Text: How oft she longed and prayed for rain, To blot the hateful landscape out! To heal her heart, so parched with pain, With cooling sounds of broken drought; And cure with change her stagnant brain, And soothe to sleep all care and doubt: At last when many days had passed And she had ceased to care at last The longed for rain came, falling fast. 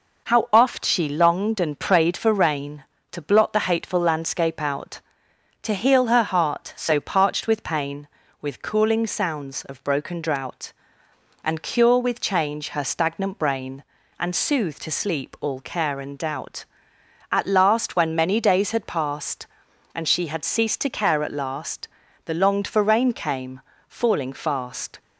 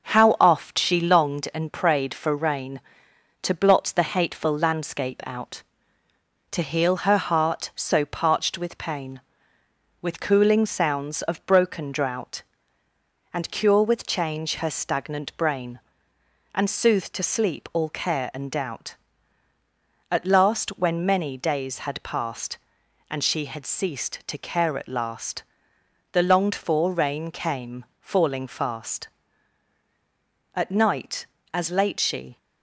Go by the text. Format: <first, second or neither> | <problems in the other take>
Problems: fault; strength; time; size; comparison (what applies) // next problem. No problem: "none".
first | starts louder than the rest; until 1.1 s; 6.5 dB // pauses between "last" and "The"; noticeable; at 25.4 s; 0.70 s long; also in the first // goes on to say "At night as late she"; strong; from 30.5 s on; 1.8 s long